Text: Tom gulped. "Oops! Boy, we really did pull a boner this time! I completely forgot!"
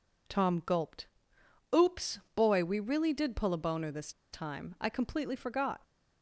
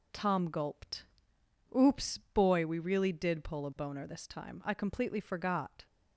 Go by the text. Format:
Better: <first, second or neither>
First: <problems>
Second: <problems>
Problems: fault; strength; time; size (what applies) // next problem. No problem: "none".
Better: second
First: pauses between "this" and "time"; slight; at 4.1 s; 0.22 s long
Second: none